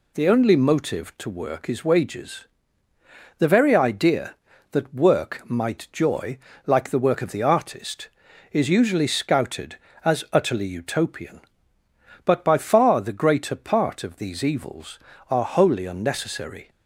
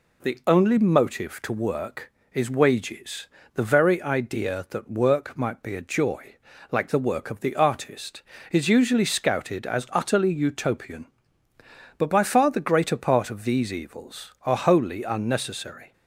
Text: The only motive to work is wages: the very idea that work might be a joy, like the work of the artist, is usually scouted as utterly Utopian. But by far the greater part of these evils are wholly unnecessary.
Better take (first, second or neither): second